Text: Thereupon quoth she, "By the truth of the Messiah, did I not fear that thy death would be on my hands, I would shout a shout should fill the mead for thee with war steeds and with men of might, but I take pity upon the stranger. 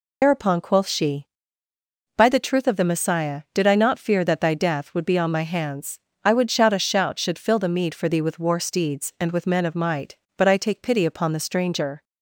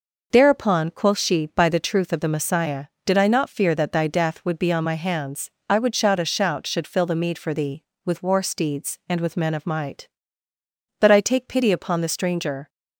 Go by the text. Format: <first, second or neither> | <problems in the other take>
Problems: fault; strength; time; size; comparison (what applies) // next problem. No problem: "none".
second | loses the start of "Thereupon"; at 0.2 s; 95 ms